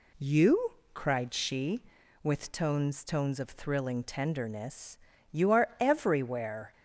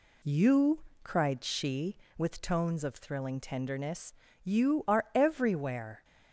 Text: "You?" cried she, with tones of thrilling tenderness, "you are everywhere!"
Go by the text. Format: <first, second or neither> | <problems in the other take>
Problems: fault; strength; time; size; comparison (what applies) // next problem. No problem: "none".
second | says "tones" twice; at 3.0 s